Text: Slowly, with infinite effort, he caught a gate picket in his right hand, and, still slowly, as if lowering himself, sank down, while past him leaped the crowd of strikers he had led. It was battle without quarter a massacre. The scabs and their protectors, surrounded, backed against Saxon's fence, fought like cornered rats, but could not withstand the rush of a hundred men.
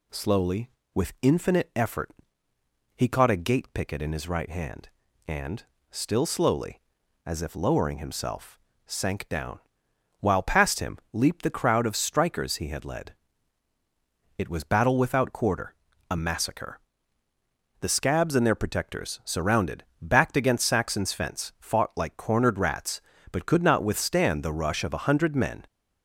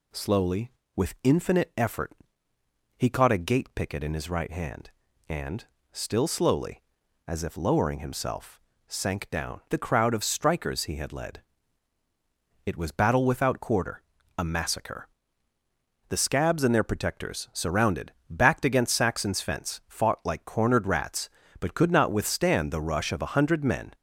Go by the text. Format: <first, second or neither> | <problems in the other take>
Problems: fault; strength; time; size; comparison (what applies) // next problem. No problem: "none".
first | skips "while past him leaped"; at 9.6 s // pauses between "quarter" and "a"; slight; at 14.0 s; 0.34 s long; slight in the first